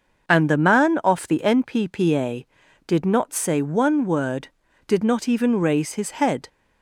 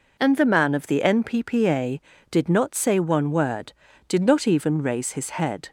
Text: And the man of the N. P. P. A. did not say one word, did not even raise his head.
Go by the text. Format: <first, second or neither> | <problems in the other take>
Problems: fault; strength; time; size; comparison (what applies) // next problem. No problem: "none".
second | starts louder than the rest; until 1.3 s; 6 dB // says "off" for "of"; at 1.0 s